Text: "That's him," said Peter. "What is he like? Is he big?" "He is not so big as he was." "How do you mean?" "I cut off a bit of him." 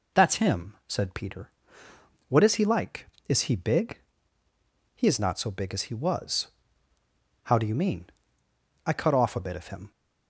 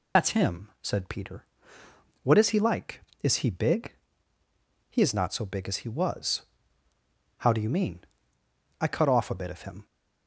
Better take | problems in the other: first | loses the start of "That's"; at 0.1 s; 60 ms

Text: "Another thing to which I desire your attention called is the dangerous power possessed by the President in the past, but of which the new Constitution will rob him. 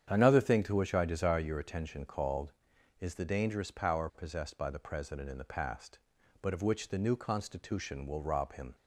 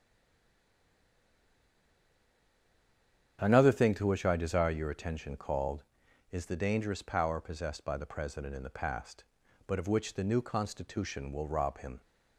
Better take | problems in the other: first | stays silent before the first word; strong; until 3.3 s; 3.3 s long // starts louder than the rest; strong; until 4.4 s; 8.5 dB; strong in the first

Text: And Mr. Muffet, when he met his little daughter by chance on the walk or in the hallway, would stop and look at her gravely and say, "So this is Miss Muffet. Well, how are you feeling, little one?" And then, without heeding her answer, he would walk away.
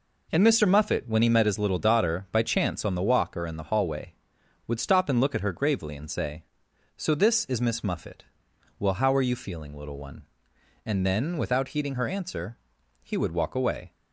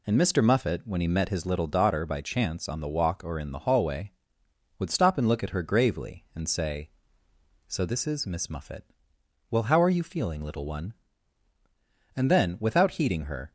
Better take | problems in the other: first | stops before "answer he would walk away"; at 13.4 s

